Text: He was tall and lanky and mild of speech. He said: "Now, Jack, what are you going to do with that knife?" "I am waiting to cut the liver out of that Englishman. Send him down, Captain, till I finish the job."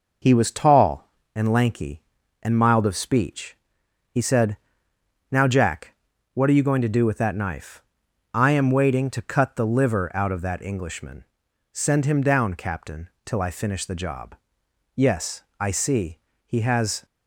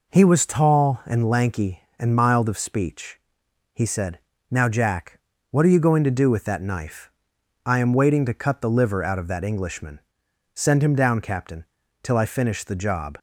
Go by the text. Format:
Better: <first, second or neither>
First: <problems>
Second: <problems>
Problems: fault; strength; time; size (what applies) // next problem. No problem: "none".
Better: second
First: goes on to say "Yes I see He has"; strong; from 14.9 s on; 2.1 s long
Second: none